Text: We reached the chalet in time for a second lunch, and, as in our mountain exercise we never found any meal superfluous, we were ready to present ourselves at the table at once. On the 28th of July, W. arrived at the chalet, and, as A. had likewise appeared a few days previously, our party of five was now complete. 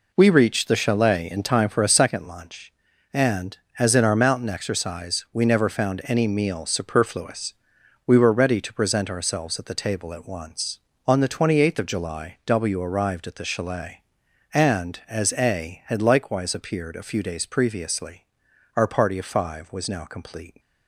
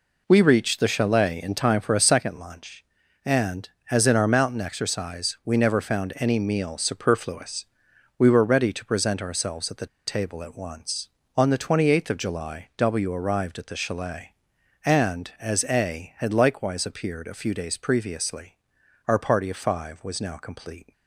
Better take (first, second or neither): first